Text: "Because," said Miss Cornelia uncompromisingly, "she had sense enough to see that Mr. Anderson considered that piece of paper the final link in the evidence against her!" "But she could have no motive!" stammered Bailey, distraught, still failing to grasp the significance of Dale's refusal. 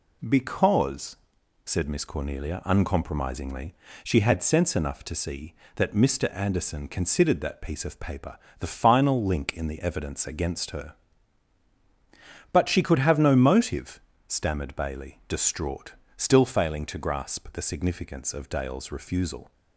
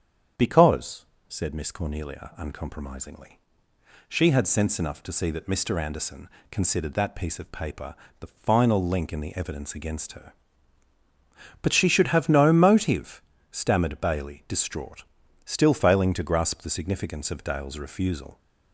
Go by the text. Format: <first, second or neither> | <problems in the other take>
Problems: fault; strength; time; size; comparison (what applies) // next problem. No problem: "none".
first | starts louder than the rest; strong; until 1.6 s; 8 dB // pauses between "Anderson" and "considered"; slight; at 6.2 s; 0.22 s long // pauses between "paper" and "the"; slight; at 7.9 s; 0.24 s long; slight in the first // says "should" for "could"; at 11.8 s